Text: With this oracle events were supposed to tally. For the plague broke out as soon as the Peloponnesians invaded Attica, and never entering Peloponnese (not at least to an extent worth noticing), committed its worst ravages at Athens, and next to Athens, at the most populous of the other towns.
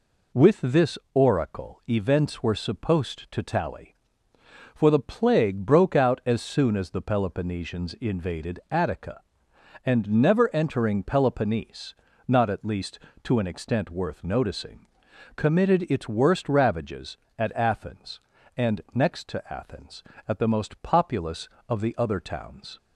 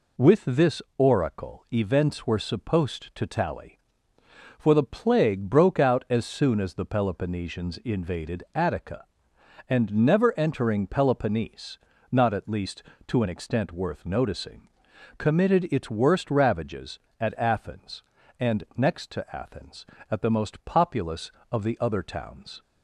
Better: neither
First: pauses between "this" and "oracle"; slight; at 0.9 s; 0.16 s long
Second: pauses between "this" and "oracle"; slight; at 0.8 s; 0.16 s long

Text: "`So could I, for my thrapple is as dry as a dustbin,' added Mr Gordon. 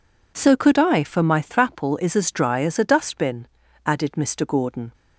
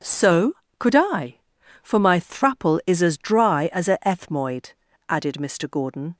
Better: first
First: none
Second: says "ethmoid" for "dustbin"; at 4.0 s

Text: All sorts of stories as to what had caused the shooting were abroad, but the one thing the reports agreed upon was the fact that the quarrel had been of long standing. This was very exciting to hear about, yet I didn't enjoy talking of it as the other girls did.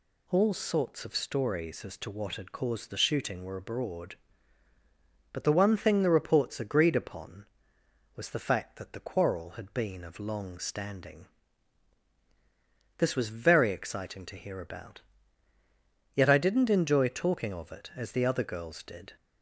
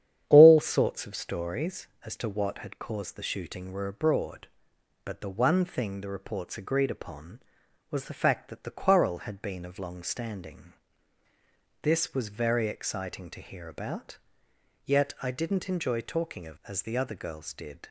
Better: first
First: none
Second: starts louder than the rest; strong; until 1.2 s; 9.5 dB // skips "it"; at 16.6 s

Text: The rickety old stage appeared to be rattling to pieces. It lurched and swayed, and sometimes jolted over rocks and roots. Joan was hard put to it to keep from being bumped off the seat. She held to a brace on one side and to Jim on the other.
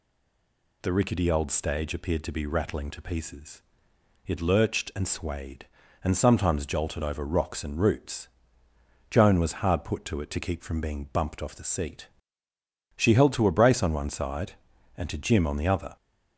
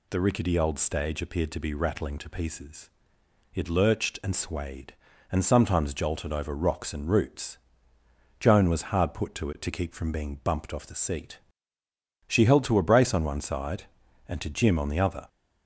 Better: second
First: stays silent before the first word; slight; until 0.8 s; 0.8 s long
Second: none

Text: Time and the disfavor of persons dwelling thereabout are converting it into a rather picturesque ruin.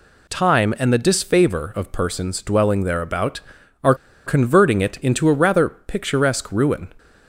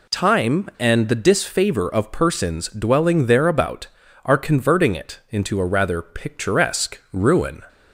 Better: second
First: pauses between "are" and "converting"; slight; at 3.9 s; 0.32 s long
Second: none

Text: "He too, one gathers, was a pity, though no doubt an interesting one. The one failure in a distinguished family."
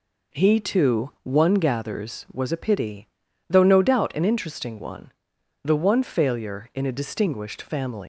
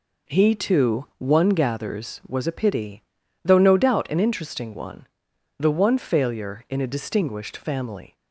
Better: second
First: leaves "family" unfinished; at 8.0 s; 115 ms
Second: none

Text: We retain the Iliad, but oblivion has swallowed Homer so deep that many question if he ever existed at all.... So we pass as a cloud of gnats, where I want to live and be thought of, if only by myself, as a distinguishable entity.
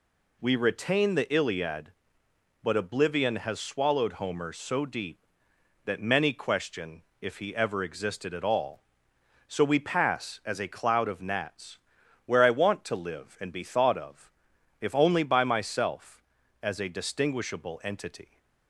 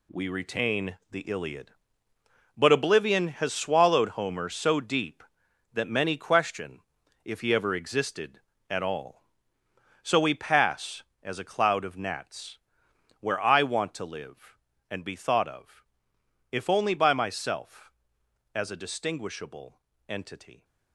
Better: first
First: pauses between "question" and "if"; slight; at 7.0 s; 0.18 s long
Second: gets quieter; strong; throughout; 10 dB // pauses between "retain" and "the"; slight; at 0.9 s; 0.16 s long // pauses between "question" and "if"; at 6.7 s; 0.44 s long // pauses between "distinguishable" and "entity"; slight; at 19.7 s; 0.30 s long

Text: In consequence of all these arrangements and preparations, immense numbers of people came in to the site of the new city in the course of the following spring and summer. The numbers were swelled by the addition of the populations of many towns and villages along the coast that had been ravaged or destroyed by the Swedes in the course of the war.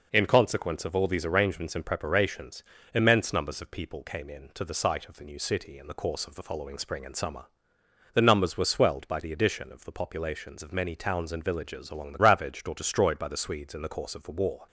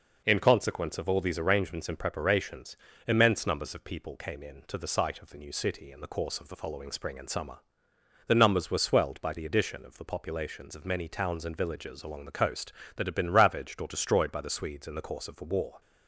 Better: second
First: skips "coast that had been"; at 12.1 s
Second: none

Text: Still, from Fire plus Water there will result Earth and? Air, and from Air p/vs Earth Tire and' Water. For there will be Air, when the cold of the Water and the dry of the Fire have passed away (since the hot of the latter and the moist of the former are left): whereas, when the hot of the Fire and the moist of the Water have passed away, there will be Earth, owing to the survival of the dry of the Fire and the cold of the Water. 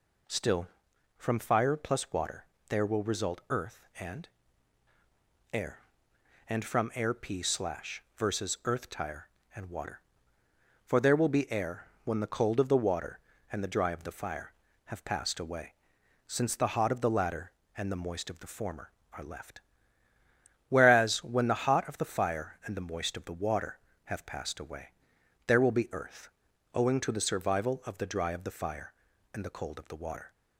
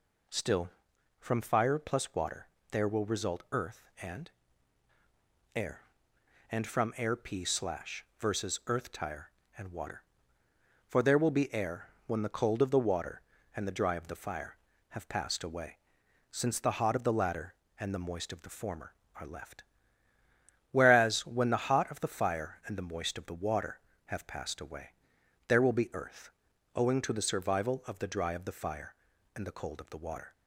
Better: neither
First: pauses between "Water" and "there"; slight; at 2.4 s; 0.24 s long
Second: pauses between "Water" and "there"; slight; at 2.4 s; 0.24 s long

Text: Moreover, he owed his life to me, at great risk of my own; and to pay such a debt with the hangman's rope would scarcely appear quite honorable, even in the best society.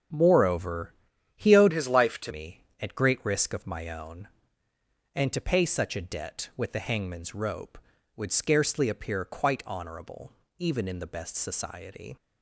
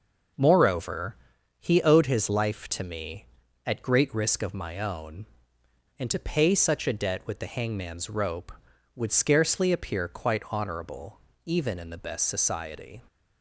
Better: second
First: starts louder than the rest; strong; until 1.5 s; 8 dB // changes voice from "his" to "to"; from 1.7 to 2.3 s; 0.6 s long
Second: none

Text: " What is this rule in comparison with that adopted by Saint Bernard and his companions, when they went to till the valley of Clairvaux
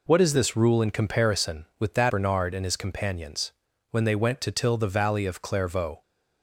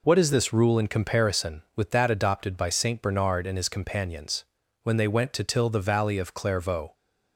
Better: second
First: skips "adopted by Saint"; at 2.0 s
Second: none

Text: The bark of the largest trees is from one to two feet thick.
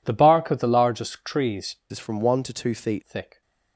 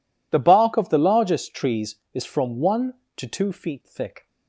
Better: second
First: changes voice from "is" to "feet"; from 1.9 to 3.0 s; 1.1 s long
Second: none

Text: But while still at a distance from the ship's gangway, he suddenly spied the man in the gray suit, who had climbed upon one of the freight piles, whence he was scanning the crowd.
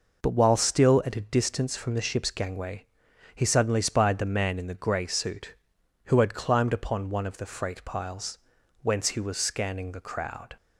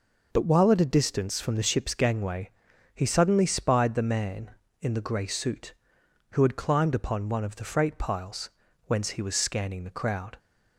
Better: first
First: none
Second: skips "still"; at 0.7 s

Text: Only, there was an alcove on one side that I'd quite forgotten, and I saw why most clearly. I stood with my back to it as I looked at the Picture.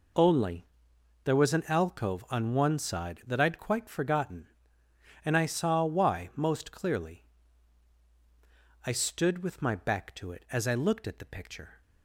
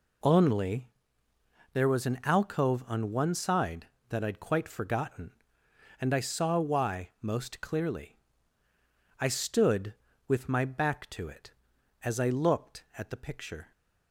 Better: neither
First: none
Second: none

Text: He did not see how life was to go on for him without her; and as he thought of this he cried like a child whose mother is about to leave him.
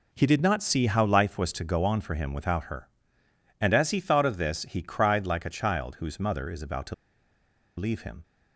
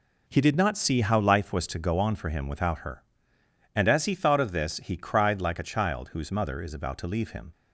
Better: second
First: pauses between "to" and "leave"; noticeable; at 6.9 s; 0.83 s long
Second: none

